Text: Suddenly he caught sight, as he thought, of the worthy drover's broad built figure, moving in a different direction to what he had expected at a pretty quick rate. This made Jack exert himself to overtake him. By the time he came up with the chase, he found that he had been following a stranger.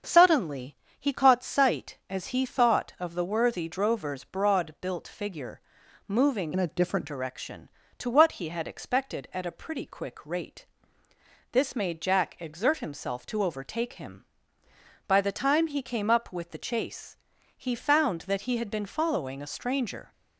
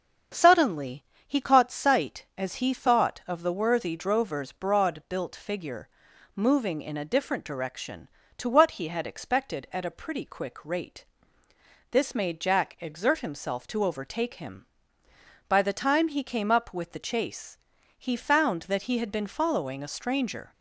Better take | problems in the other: second | starts louder than the rest; until 1.2 s; 6.5 dB; also in the second // pauses between "Suddenly" and "he"; slight; at 0.7 s; 0.22 s long; slight in the second // changes voice from "in" to "different"; from 6.5 to 7.0 s; 0.5 s long

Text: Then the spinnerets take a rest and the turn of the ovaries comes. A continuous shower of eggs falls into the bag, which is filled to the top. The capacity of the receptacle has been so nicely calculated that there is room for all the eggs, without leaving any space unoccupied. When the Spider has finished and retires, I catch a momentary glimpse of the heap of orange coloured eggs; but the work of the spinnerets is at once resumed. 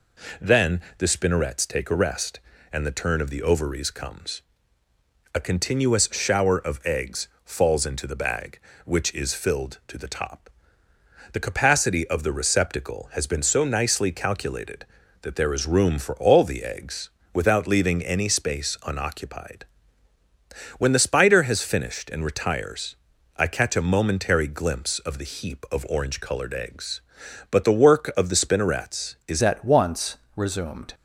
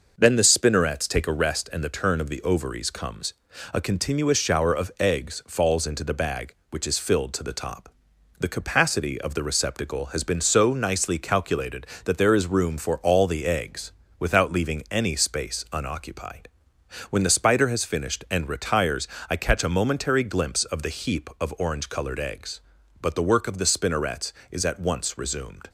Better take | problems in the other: second | pauses between "Then" and "the"; slight; at 0.8 s; 0.16 s long // pauses between "eggs" and "falls"; slight; at 7.2 s; 0.18 s long // changes voice at "at"; from 29.4 s on; 1.5 s long // pauses between "once" and "resumed"; slight; at 30.1 s; 0.18 s long

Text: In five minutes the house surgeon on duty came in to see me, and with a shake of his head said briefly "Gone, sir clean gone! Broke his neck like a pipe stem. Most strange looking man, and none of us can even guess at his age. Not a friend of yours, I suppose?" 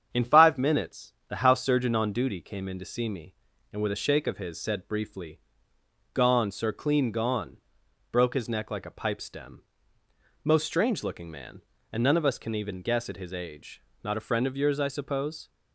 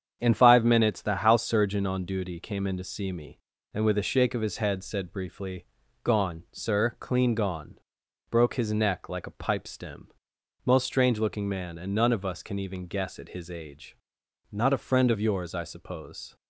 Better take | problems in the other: second | starts louder than the rest; strong; until 1.1 s; 8 dB; strong in the second // pauses between "minutes" and "the"; slight; at 1.1 s; 0.16 s long // skips "head"; at 4.5 s // pauses between "briefly" and "Gone"; noticeable; at 5.3 s; 0.76 s long; also in the second

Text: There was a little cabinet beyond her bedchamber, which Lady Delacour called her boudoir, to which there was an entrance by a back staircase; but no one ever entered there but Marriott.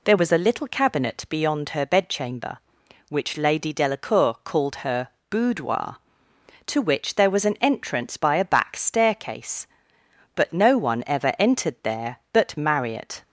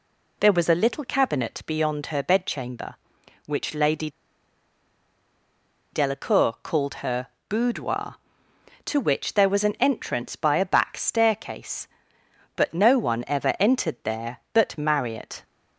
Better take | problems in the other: first | pauses between "Lady" and "Delacour"; strong; at 4.0 s; 1.8 s long // pauses between "her" and "boudoir"; slight; at 7.2 s; 0.20 s long; slight in the first

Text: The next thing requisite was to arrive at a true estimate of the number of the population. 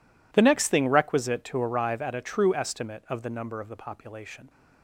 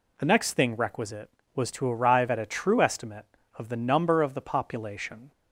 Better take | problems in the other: second | skips "was"; at 1.4 s

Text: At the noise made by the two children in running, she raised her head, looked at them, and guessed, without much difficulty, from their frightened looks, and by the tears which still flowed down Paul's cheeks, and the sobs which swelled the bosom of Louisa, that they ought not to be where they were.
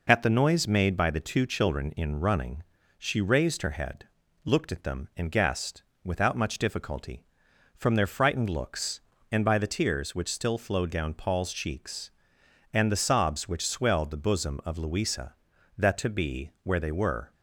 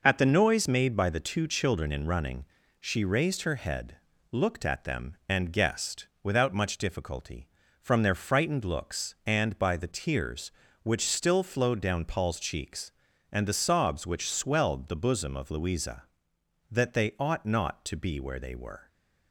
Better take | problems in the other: second | skips "they ought not"; at 15.9 s

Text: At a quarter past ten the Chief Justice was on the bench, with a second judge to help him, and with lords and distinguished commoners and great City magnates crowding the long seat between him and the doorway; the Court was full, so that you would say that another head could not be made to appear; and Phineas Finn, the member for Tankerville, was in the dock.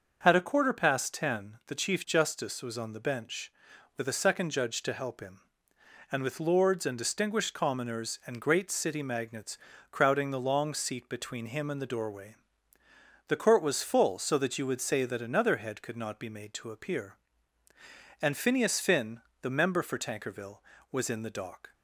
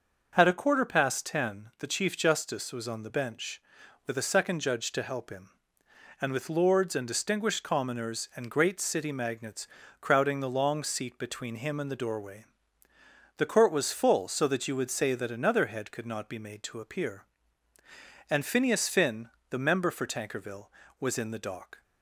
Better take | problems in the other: neither | starts louder than the rest; the same in both // pauses between "magnates" and "crowding"; slight; the same in both

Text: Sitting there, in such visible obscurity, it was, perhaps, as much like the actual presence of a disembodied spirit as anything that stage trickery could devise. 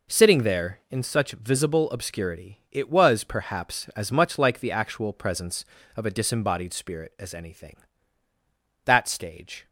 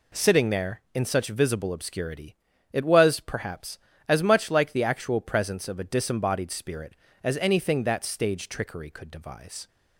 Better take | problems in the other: second | stops before "trickery could devise"; at 9.6 s

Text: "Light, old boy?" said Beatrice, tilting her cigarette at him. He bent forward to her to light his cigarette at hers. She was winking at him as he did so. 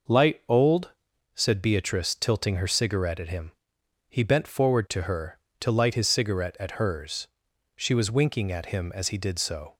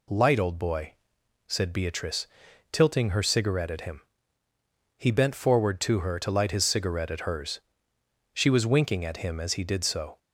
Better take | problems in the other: second | skips "boy"; at 1.1 s

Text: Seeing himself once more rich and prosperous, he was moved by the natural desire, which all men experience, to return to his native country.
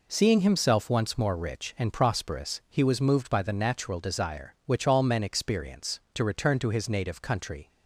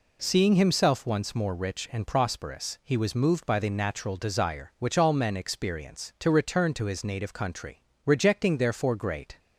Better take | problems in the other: first | goes on to say "Rejecting therefore great"; from 8.0 s on; 1.3 s long

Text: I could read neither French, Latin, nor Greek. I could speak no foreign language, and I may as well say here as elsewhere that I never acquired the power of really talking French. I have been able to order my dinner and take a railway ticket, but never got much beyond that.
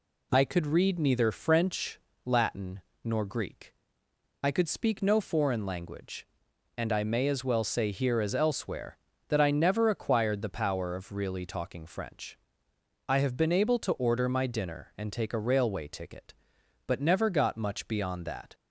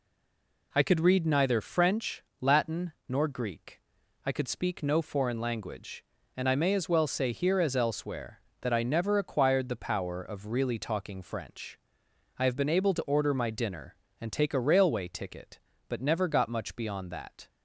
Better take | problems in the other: first | stays silent before the first word; slight; until 0.7 s; 0.7 s long

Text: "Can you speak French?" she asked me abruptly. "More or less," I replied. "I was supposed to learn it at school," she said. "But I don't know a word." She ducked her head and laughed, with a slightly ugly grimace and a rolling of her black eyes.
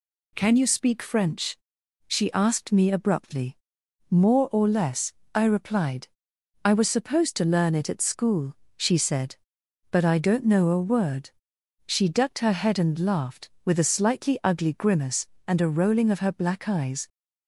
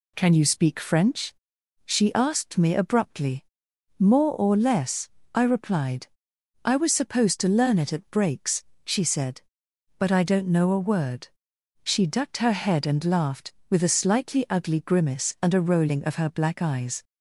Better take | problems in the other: first | says "breaks" for "school"; at 8.0 s

